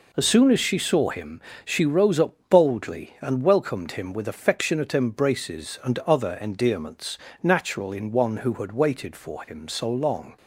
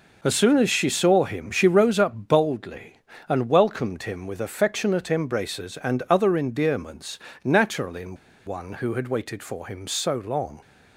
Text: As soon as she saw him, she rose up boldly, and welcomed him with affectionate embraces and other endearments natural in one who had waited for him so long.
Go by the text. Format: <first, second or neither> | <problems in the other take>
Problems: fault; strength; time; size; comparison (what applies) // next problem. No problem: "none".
first | pauses between "endearments" and "natural"; slight; at 7.1 s; 0.24 s long; slight in the first // pauses between "in" and "one"; slight; at 8.1 s; 0.30 s long